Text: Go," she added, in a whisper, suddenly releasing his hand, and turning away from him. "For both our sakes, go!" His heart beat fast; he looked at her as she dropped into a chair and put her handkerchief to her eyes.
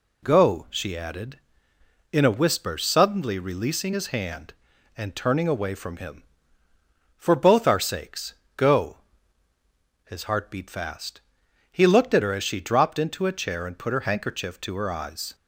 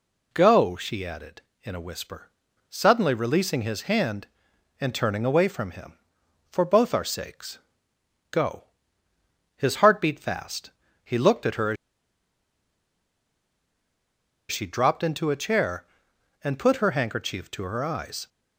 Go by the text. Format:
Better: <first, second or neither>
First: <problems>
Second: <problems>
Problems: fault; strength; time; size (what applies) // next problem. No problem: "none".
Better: first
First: none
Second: pauses between "as" and "she"; strong; at 11.7 s; 2.7 s long